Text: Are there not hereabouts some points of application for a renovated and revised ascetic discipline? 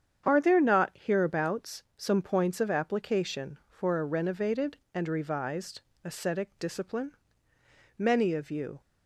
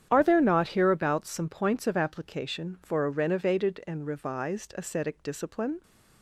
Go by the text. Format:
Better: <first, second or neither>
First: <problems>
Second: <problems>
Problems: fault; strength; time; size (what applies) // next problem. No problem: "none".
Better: second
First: starts louder than the rest; strong; until 1.2 s; 8 dB // pauses between "hereabouts" and "some"; slight; at 1.8 s; 0.16 s long // pauses between "revised" and "ascetic"; slight; at 5.8 s; 0.20 s long // goes on to say "Many of you"; noticeable; from 7.9 s on; 0.82 s long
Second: starts louder than the rest; strong; until 1.1 s; 9 dB